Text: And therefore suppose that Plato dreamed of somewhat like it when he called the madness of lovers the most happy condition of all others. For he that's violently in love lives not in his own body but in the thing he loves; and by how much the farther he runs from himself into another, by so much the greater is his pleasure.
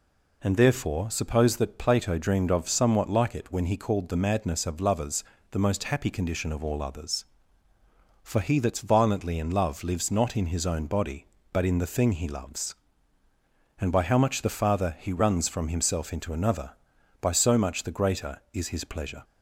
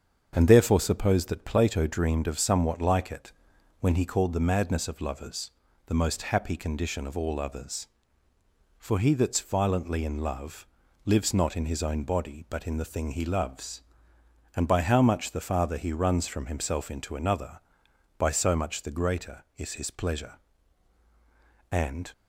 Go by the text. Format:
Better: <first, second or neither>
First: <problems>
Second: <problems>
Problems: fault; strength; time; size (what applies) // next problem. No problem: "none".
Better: first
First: pauses between "lovers" and "the"; slight; at 5.2 s; 0.28 s long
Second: starts louder than the rest; strong; until 1.3 s; 7 dB // pauses between "it" and "when"; noticeable; at 3.3 s; 0.48 s long // pauses between "lovers" and "the"; slight; at 5.5 s; 0.34 s long // pauses between "love" and "lives"; at 10.6 s; 0.38 s long // goes on to say "And"; slight; from 21.6 s on; 0.42 s long